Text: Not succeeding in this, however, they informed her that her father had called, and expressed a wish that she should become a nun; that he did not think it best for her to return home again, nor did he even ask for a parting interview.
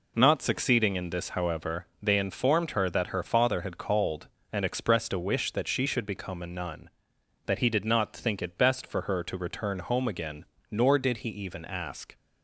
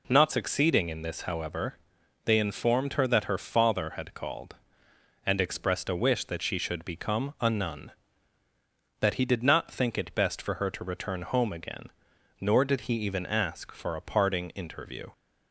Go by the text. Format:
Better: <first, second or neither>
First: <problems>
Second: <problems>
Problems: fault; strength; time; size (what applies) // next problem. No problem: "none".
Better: second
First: stops before "for a parting interview"; at 12.1 s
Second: none